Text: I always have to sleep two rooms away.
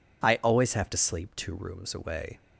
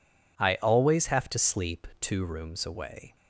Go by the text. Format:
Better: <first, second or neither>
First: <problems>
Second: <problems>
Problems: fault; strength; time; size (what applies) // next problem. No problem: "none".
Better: neither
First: none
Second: none